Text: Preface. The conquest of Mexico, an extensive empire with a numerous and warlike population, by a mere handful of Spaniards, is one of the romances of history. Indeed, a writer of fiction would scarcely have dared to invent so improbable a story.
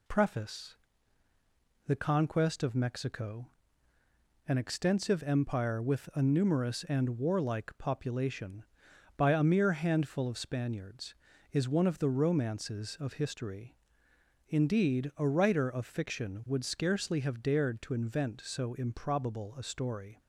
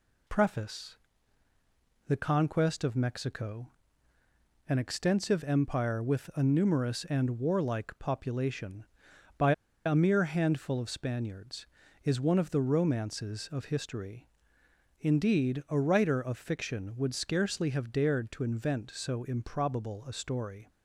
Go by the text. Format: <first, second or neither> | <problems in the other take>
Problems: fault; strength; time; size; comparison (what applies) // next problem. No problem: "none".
first | pauses between "by" and "a"; slight; at 9.5 s; 0.32 s long